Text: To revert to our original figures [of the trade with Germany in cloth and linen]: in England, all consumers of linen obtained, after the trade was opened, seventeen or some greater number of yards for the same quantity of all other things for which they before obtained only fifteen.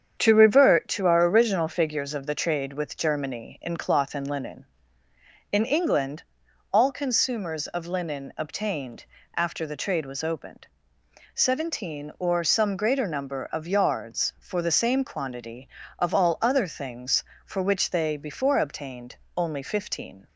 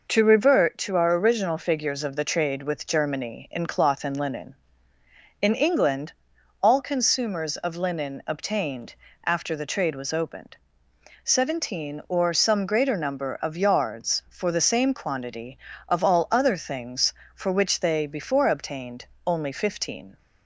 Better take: second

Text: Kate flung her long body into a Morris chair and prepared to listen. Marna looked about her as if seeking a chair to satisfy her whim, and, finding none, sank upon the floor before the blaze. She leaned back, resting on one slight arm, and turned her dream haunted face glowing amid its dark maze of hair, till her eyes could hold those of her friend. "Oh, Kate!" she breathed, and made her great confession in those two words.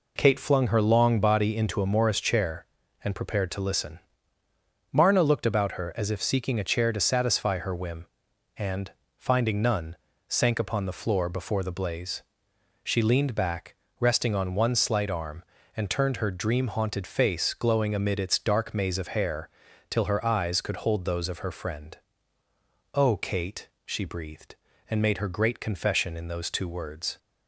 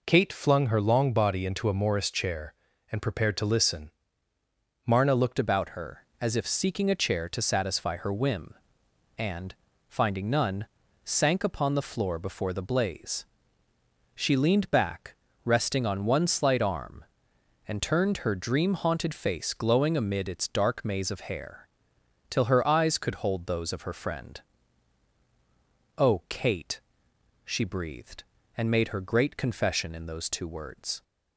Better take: first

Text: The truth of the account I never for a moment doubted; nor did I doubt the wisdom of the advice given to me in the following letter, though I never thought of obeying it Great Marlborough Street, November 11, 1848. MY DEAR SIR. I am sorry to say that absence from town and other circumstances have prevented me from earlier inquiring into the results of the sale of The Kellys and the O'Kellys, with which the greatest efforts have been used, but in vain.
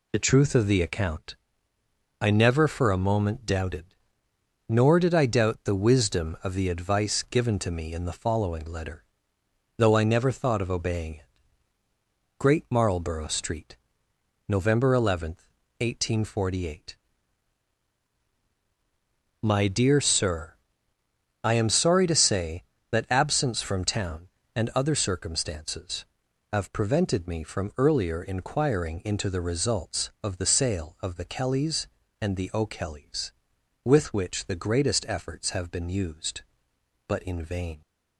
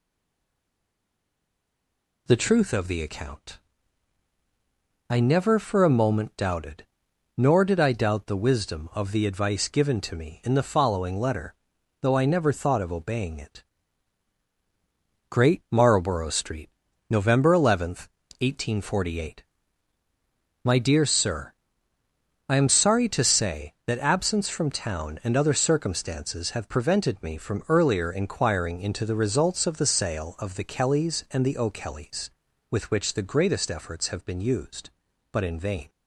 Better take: first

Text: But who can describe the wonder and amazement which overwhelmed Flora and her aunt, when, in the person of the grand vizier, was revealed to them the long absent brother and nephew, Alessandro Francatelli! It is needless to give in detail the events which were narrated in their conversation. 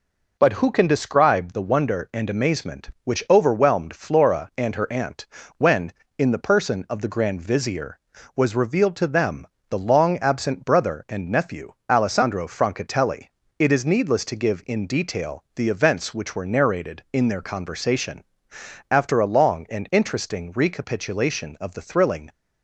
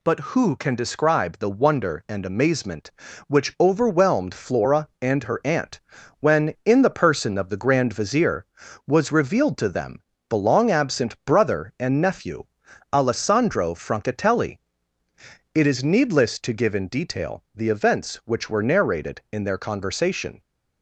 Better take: second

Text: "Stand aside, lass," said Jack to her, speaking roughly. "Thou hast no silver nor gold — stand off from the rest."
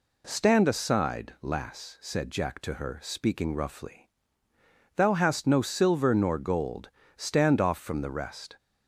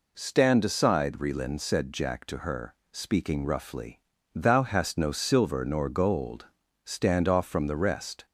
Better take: first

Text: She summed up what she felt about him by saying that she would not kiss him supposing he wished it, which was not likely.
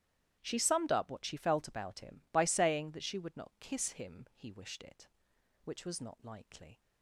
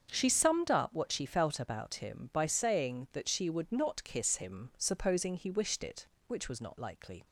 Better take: second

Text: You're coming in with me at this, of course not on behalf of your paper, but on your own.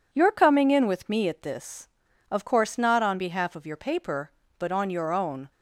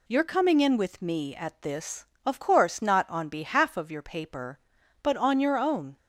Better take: neither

